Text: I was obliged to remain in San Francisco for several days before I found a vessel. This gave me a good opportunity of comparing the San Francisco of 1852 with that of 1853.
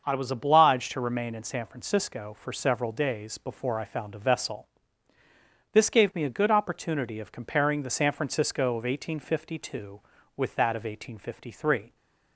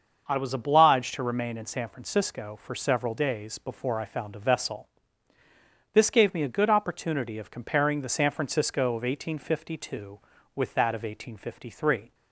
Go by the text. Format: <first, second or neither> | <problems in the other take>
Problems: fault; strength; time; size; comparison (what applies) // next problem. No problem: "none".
neither | starts louder than the rest; the same in both